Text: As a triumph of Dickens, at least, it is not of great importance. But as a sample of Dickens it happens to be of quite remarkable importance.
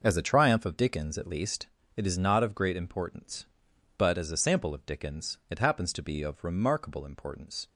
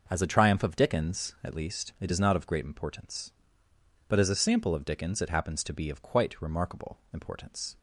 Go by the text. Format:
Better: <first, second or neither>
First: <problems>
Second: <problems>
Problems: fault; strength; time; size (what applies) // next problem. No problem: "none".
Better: second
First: skips "quite"; at 6.4 s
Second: none